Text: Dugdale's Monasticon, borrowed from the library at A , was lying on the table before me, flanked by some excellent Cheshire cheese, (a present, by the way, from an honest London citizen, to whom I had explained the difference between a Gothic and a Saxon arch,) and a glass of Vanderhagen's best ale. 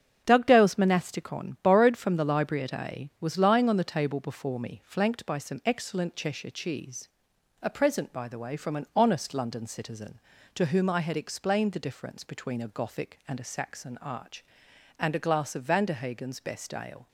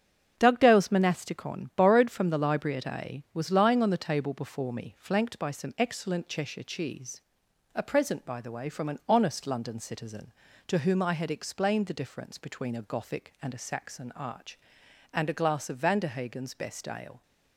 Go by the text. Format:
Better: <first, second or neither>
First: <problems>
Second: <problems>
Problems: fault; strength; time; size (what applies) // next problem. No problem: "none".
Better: neither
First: starts louder than the rest; strong; until 1.2 s; 7 dB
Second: starts louder than the rest; strong; until 1.3 s; 7 dB